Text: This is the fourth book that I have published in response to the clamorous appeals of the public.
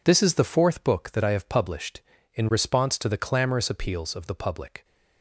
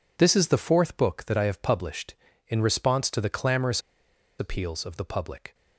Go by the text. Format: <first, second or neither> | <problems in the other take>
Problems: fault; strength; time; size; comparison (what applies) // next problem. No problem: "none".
first | pauses between "clamorous" and "appeals"; noticeable; at 3.8 s; 0.58 s long